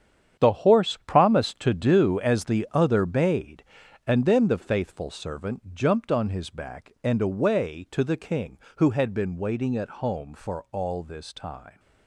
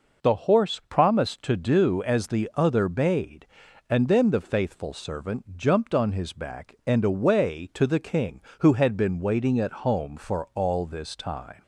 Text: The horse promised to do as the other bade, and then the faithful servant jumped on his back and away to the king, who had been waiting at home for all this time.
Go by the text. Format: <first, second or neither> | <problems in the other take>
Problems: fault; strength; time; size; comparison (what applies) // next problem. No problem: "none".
second | gets quieter; strong; throughout; 11.5 dB